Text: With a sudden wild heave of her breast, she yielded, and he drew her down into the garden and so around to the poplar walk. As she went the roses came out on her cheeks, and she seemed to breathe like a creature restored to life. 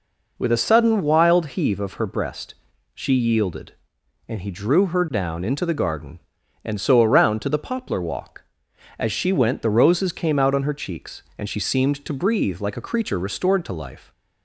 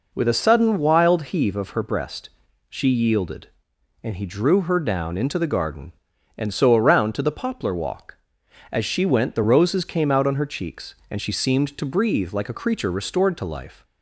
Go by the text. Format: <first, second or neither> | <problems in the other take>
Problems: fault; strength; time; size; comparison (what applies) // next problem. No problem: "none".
neither | none